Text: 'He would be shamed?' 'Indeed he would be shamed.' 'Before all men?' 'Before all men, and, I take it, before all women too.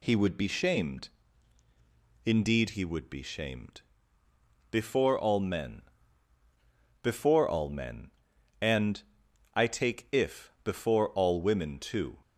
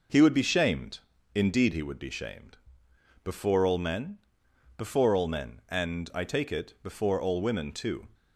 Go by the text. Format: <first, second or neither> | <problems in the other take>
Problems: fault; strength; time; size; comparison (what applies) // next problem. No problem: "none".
second | says "if" for "it"; at 10.1 s